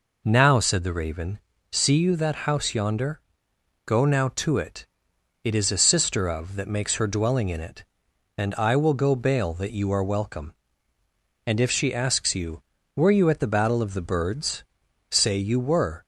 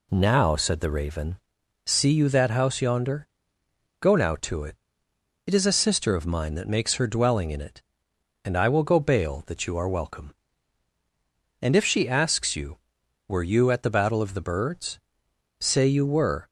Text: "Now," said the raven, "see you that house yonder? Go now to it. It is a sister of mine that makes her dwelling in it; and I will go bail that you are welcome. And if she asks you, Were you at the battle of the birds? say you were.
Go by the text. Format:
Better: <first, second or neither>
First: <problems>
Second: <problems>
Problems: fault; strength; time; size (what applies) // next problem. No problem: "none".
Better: second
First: skips "mine"; at 6.5 s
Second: none